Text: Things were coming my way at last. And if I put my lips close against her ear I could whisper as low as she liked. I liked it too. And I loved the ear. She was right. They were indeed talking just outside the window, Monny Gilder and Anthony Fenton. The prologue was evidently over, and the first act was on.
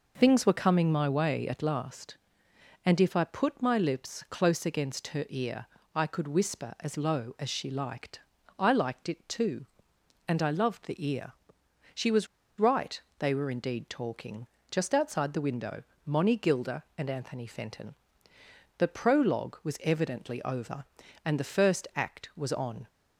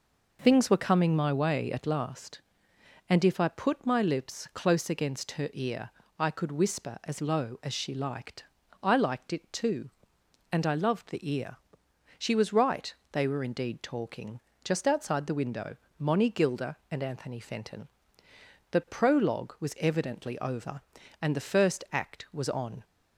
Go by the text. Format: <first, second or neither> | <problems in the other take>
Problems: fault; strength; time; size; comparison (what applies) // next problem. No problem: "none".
second | pauses between "ear" and "I"; slight; at 5.6 s; 0.28 s long; slight in the second // pauses between "was" and "right"; slight; at 12.2 s; 0.33 s long // pauses between "talking" and "just"; slight; at 14.4 s; 0.22 s long; slight in the second